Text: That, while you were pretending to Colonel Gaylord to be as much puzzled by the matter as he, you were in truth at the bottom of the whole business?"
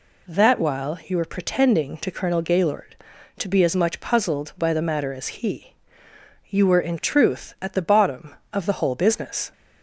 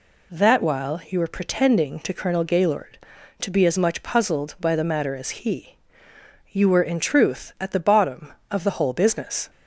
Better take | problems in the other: neither | none

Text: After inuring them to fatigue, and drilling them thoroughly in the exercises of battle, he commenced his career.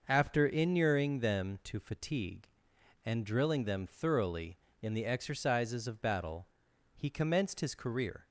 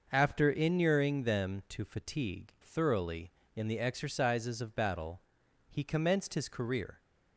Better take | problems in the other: first | skips "and drilling them"; at 2.5 s

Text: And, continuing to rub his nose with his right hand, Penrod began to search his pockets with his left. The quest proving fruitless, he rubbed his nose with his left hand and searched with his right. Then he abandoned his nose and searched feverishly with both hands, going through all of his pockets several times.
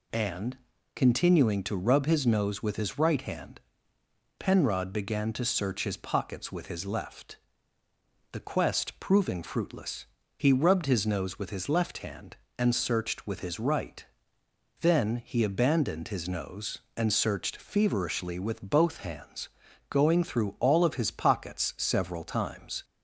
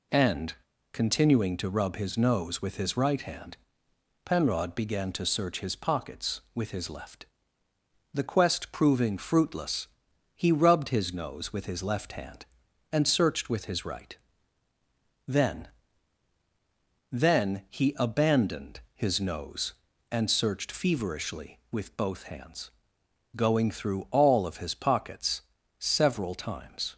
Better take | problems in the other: first | says "Then" twice; at 17.1 s // pauses between "pockets" and "several"; at 25.4 s; 0.38 s long

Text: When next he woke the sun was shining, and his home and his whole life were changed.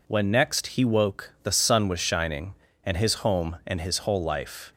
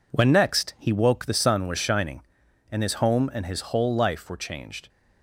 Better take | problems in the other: second | stops before "were changed"; at 4.7 s

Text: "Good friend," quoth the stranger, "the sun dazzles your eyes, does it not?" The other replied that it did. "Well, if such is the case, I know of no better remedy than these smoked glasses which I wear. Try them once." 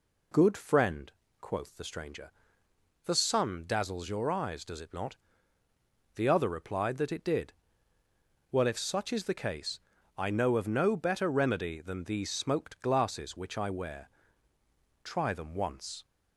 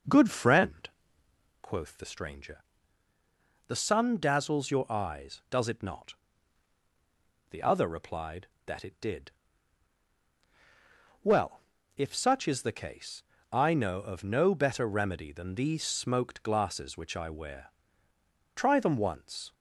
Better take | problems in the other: neither | none

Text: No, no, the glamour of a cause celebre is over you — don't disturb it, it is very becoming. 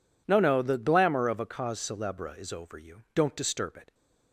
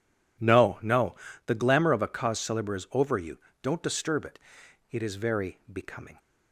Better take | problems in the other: second | stops before "it is very becoming"; at 3.9 s

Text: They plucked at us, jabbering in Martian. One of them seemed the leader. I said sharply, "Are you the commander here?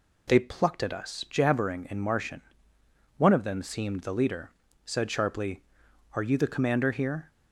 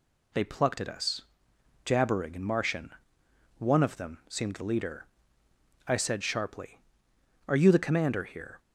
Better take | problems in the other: second | skips "I"; at 4.6 s

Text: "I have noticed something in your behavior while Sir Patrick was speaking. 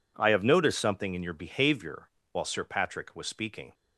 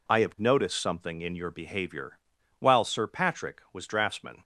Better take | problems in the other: first | pauses between "behavior" and "while"; at 2.1 s; 0.40 s long; slight in the first // says "draftsman" for "speaking"; at 3.8 s

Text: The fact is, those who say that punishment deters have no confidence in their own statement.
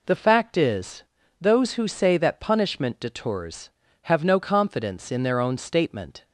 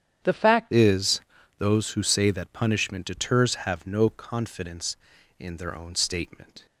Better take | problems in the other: first | starts louder than the rest; strong; until 1.6 s; 9 dB // changes voice at "is"; from 0.7 s on; 5.9 s long

